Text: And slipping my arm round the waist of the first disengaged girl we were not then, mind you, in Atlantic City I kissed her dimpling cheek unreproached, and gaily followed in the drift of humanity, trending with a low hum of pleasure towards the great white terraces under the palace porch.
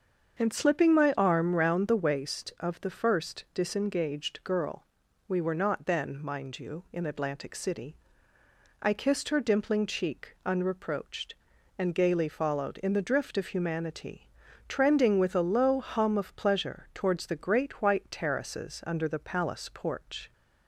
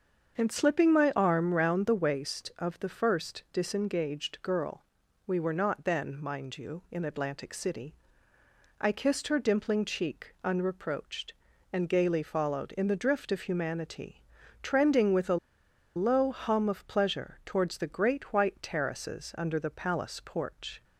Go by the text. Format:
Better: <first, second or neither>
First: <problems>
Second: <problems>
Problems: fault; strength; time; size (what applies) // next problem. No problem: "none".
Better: first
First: starts louder than the rest; until 1.4 s; 7 dB // pauses between "girl" and "we"; at 4.8 s; 0.44 s long // pauses between "City" and "I"; noticeable; at 7.9 s; 0.84 s long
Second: starts louder than the rest; until 1.4 s; 7 dB // pauses between "girl" and "we"; at 4.8 s; 0.44 s long // pauses between "City" and "I"; noticeable; at 7.9 s; 0.84 s long // pauses between "a" and "low"; noticeable; at 15.3 s; 0.59 s long